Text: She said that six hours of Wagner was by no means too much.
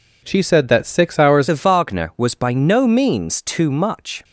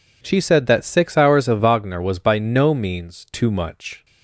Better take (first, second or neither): second